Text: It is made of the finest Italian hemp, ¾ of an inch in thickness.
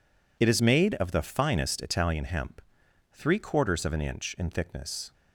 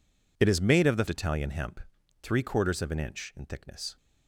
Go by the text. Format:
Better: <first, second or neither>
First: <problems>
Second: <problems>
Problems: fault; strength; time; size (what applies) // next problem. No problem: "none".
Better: first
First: none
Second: skips "finest"; at 1.0 s